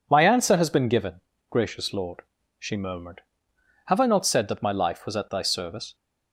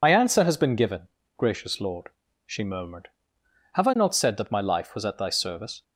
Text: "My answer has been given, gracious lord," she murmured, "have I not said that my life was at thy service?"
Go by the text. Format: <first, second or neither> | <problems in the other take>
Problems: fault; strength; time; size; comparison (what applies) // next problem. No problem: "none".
first | loses the start of "My"; at 0.0 s; 60 ms